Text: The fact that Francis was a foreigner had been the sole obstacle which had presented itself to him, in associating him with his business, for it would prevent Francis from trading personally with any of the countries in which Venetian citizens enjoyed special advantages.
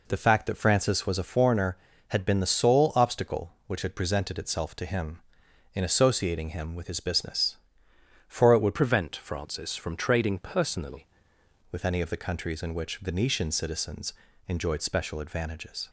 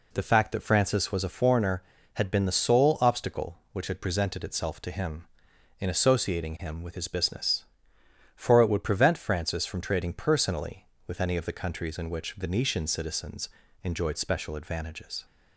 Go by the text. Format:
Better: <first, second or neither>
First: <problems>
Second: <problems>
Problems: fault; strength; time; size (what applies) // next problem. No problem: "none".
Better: second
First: changes voice from "prevent" to "personally"; from 8.7 to 11.0 s; 2.3 s long // pauses between "citizens" and "enjoyed"; slight; at 14.1 s; 0.34 s long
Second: pauses between "citizens" and "enjoyed"; slight; at 13.4 s; 0.34 s long